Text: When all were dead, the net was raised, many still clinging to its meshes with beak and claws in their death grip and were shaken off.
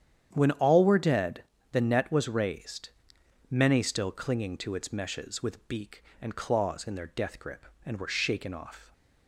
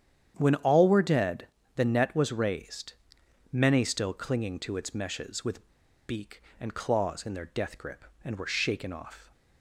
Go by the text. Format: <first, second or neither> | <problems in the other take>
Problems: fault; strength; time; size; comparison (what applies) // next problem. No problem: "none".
first | starts louder than the rest; strong; until 1.3 s; 9 dB; strong in the first // pauses between "with" and "beak"; at 5.7 s; 0.37 s long